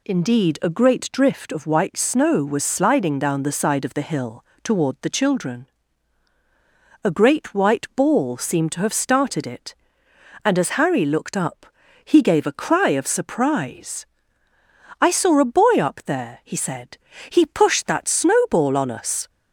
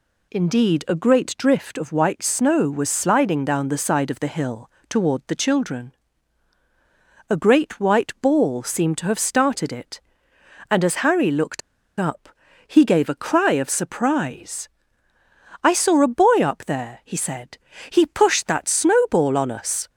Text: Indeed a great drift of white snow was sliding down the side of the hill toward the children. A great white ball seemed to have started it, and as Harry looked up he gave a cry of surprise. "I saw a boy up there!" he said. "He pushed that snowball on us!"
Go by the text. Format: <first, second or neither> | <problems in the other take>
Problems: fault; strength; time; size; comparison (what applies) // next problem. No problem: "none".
first | pauses between "hill" and "toward"; slight; at 4.6 s; 0.20 s long; slight in the first // pauses between "looked" and "up"; at 11.6 s; 0.38 s long // pauses between "up" and "he"; slight; at 12.2 s; 0.36 s long; slight in the first